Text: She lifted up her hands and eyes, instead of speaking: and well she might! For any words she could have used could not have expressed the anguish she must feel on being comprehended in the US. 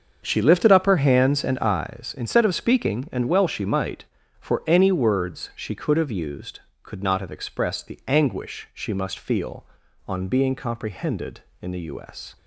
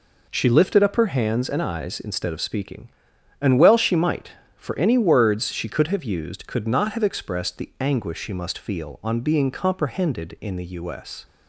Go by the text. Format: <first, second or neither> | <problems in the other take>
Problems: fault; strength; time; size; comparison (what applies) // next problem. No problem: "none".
second | starts louder than the rest; until 2.0 s; 6.5 dB